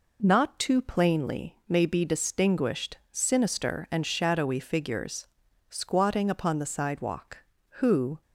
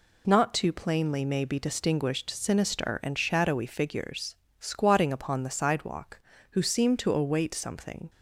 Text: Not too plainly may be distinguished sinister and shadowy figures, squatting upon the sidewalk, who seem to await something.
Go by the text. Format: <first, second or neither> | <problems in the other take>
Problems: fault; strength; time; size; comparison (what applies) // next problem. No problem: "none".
second | stops before "seem to await something"; at 8.2 s